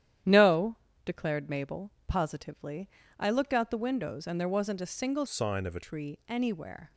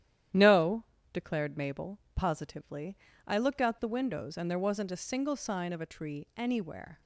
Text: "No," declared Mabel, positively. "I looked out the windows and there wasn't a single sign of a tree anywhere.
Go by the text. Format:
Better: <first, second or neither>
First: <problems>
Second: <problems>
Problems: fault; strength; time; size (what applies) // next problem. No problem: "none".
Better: second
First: starts louder than the rest; strong; until 1.5 s; 10.5 dB // changes voice from "sign" to "a"; from 5.2 to 5.8 s; 0.6 s long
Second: starts louder than the rest; strong; until 1.6 s; 11 dB